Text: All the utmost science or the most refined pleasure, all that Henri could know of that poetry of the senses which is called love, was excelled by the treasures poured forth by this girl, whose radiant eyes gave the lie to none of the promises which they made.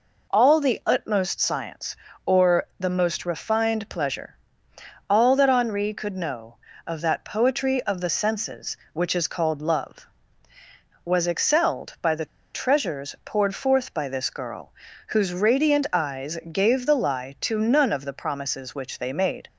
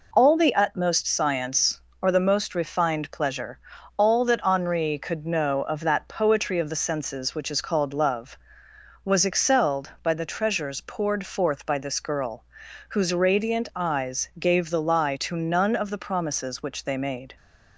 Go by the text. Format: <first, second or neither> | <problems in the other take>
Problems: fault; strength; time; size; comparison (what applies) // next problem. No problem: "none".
second | pauses between "the" and "treasures"; slight; at 12.2 s; 0.28 s long